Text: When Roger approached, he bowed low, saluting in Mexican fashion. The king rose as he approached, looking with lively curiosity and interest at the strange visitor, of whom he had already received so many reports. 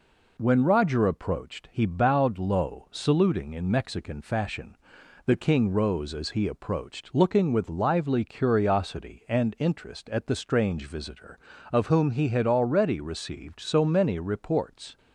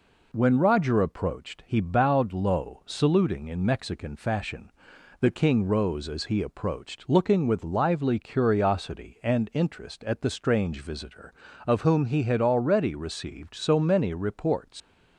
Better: first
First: none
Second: leaves "reports" unfinished; at 14.8 s; 115 ms

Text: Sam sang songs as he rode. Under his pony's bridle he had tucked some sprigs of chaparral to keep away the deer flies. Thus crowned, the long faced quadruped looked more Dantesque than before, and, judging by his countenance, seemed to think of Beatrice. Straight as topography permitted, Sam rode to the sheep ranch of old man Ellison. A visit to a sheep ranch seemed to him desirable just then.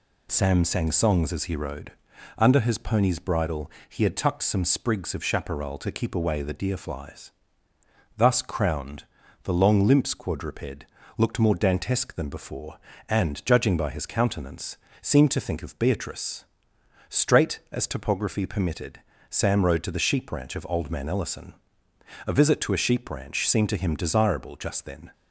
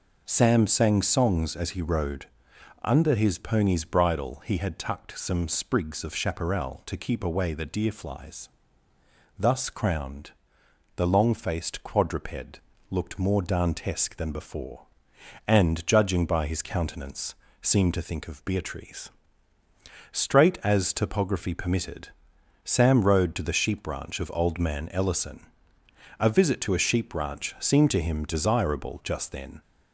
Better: second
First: pauses between "bridle" and "he"; slight; at 3.6 s; 0.18 s long // says "limps" for "faced"; at 9.8 s // pauses between "quadruped" and "looked"; slight; at 10.8 s; 0.32 s long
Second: pauses between "quadruped" and "looked"; slight; at 12.5 s; 0.32 s long

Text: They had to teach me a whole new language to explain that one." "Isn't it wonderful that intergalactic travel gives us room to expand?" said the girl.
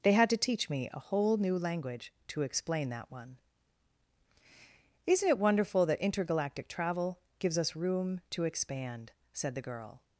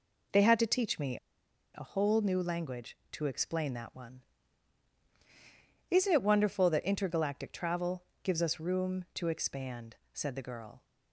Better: first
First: pauses between "travel" and "gives"; slight; at 7.1 s; 0.18 s long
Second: pauses between "me" and "a"; noticeable; at 1.1 s; 0.56 s long // pauses between "travel" and "gives"; slight; at 8.0 s; 0.18 s long

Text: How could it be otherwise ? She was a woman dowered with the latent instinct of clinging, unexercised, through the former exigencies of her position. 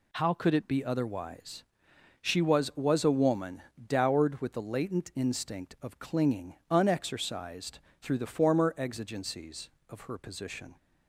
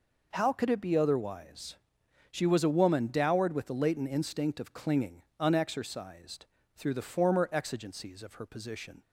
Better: second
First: says "was" twice; at 2.7 s // pauses between "woman" and "dowered"; slight; at 3.6 s; 0.22 s long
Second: none

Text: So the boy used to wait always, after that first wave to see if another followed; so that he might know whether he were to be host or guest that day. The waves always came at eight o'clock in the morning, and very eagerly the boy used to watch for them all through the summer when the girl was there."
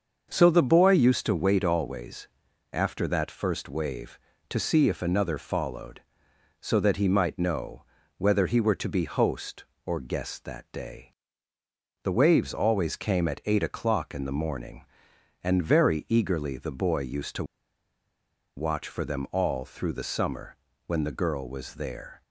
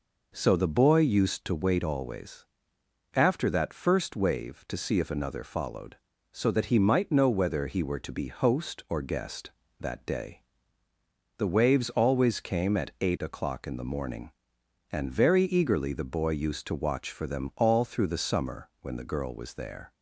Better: second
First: starts louder than the rest; until 1.3 s; 6.5 dB // pauses between "know" and "whether"; slight; at 7.8 s; 0.36 s long // pauses between "to" and "watch"; at 17.4 s; 1.1 s long // pauses between "summer" and "when"; slight; at 20.5 s; 0.32 s long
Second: none

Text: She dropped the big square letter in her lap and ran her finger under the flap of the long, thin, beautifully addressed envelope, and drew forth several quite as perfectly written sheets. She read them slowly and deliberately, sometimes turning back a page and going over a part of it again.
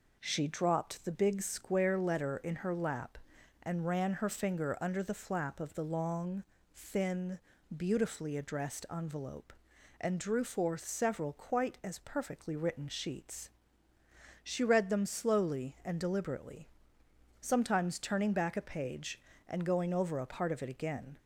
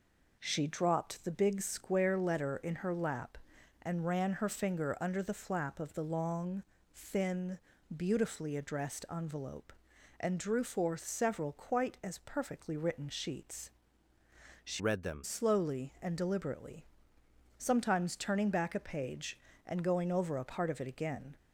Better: first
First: none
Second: changes voice from "read" to "them"; from 14.7 to 15.2 s; 0.5 s long

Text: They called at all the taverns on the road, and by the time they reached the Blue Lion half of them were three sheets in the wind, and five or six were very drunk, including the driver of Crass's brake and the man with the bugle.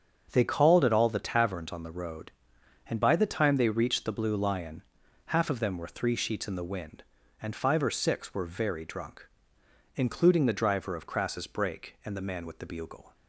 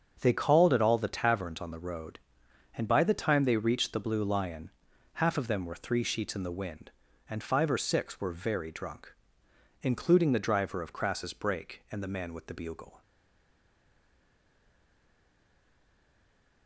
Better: first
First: starts louder than the rest; until 1.3 s; 7 dB // pauses between "Lion" and "half"; at 4.8 s; 0.44 s long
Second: starts louder than the rest; until 1.2 s; 7 dB // pauses between "Lion" and "half"; at 4.7 s; 0.44 s long // stays silent after the last word; strong; from 13.0 s on; 3.6 s long

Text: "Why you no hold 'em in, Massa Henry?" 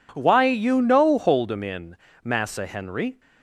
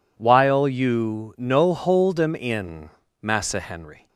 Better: first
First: none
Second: says "While" for "Why"; at 0.1 s

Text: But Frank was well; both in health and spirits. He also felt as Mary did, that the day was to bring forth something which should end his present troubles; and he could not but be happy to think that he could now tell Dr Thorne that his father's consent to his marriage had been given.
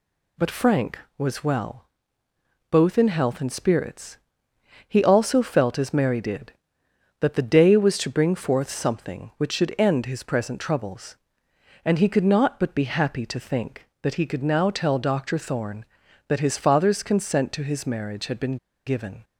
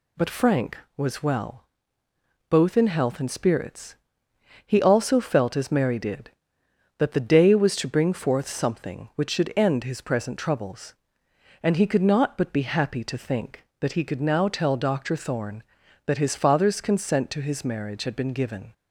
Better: second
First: pauses between "been" and "given"; slight; at 18.5 s; 0.29 s long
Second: none

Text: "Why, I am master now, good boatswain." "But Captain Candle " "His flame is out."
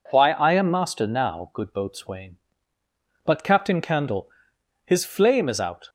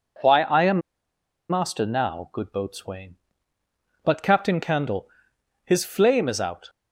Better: first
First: none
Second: pauses between "am" and "master"; noticeable; at 0.8 s; 0.68 s long

